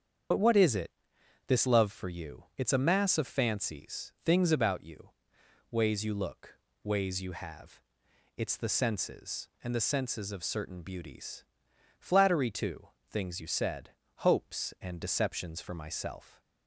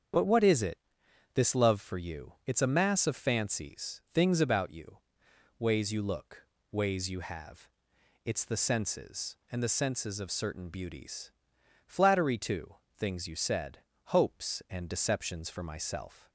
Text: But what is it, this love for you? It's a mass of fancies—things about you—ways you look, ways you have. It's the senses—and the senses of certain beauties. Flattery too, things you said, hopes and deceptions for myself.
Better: second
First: loses the start of "But"; at 0.3 s; 40 ms // starts louder than the rest; strong; until 1.9 s; 7.5 dB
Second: starts louder than the rest; strong; until 1.7 s; 8 dB

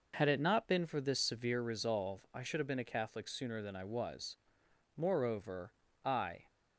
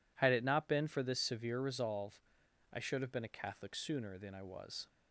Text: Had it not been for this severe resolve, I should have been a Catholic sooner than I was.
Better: second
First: goes on to say "Moreover I"; from 4.9 s on; 1.4 s long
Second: none

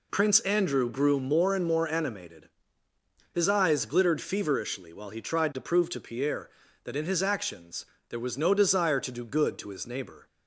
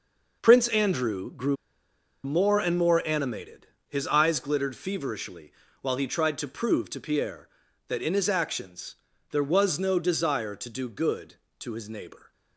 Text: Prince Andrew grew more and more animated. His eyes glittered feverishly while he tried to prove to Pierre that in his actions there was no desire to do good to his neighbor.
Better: first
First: pauses between "actions" and "there"; slight; at 7.8 s; 0.24 s long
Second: pauses between "grew" and "more"; noticeable; at 1.5 s; 0.69 s long // pauses between "feverishly" and "while"; slight; at 5.5 s; 0.28 s long // pauses between "actions" and "there"; slight; at 8.9 s; 0.34 s long

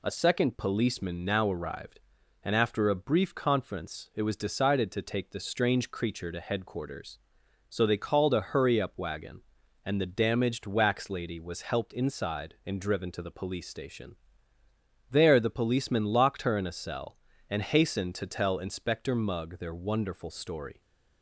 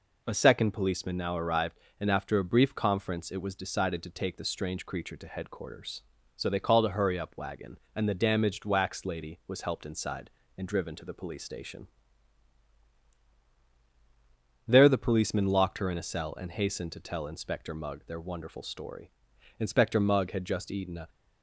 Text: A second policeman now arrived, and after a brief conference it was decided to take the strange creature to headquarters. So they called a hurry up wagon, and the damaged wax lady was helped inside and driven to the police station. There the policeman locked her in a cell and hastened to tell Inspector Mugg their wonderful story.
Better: first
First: none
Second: goes on to say "Inspector Mugg had just eaten a"; from 19.5 s on; 1.5 s long

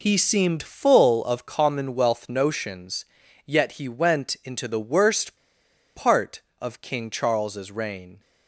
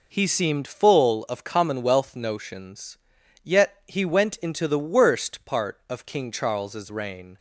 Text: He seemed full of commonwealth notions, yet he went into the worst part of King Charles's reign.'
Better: second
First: pauses between "worst" and "part"; noticeable; at 5.3 s; 0.60 s long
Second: none

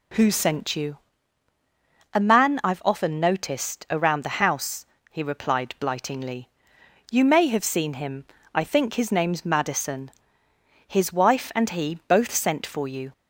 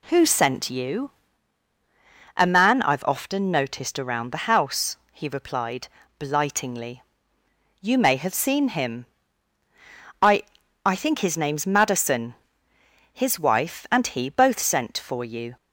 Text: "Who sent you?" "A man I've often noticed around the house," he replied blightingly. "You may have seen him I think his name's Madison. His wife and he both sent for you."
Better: first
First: pauses between "him" and "I"; slight; at 8.2 s; 0.28 s long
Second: pauses between "replied" and "blightingly"; slight; at 5.8 s; 0.30 s long // pauses between "him" and "I"; at 9.0 s; 1.1 s long // says "I" twice; at 10.8 s

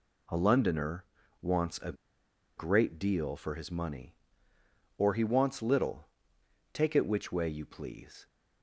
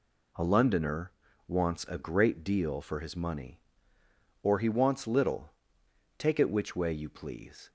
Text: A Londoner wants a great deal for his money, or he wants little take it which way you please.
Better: second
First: pauses between "Londoner" and "wants"; slight; at 1.0 s; 0.36 s long // pauses between "a" and "great"; noticeable; at 1.9 s; 0.64 s long // pauses between "little" and "take"; noticeable; at 6.0 s; 0.64 s long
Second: pauses between "Londoner" and "wants"; slight; at 1.1 s; 0.35 s long // pauses between "little" and "take"; noticeable; at 5.5 s; 0.64 s long

